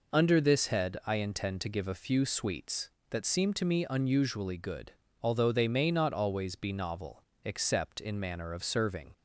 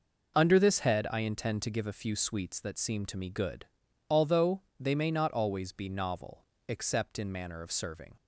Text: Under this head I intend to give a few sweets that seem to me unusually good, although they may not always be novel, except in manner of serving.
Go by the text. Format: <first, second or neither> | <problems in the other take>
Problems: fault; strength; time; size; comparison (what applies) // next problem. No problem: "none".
first | skips "unusually"; at 3.2 s // pauses between "although" and "they"; slight; at 4.6 s; 0.18 s long